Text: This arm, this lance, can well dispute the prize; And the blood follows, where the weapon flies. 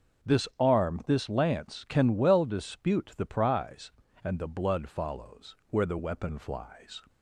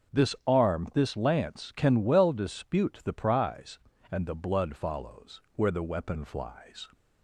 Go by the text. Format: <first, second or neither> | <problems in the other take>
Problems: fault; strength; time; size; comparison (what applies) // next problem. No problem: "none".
neither | starts louder than the rest; strong; the same in both